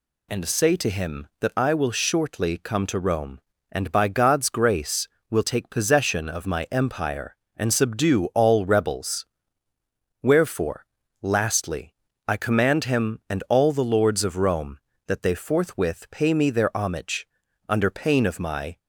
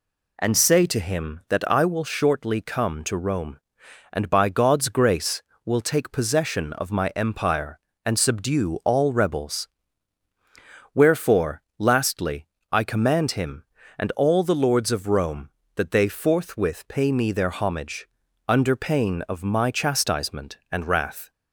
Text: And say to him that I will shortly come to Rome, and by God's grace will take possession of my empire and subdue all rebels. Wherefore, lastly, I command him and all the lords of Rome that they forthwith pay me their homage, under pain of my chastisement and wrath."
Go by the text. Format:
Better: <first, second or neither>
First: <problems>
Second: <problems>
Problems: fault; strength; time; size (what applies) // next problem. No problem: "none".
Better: second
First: stops before "chastisement and wrath"; at 18.7 s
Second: none